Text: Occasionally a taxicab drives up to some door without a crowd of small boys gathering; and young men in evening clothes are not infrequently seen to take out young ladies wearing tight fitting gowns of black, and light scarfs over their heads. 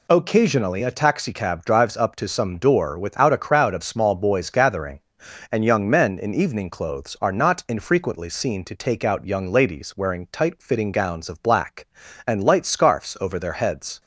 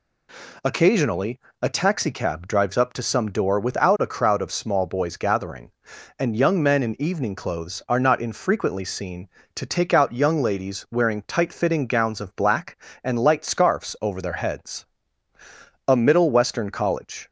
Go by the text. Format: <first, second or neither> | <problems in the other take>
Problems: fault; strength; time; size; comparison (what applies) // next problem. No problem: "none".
first | pauses between "Occasionally" and "a"; slight; at 1.3 s; 0.20 s long // goes on to say "A Middle Western college"; from 15.8 s on; 1.4 s long